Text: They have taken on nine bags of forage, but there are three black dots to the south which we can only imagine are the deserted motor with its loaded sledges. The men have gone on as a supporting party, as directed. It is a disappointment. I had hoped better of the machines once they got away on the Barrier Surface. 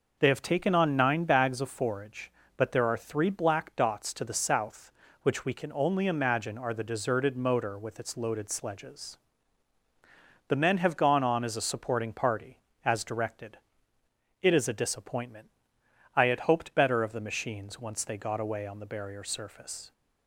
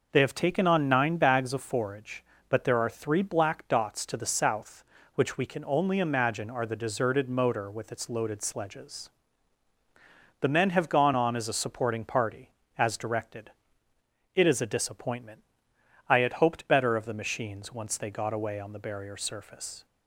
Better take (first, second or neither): neither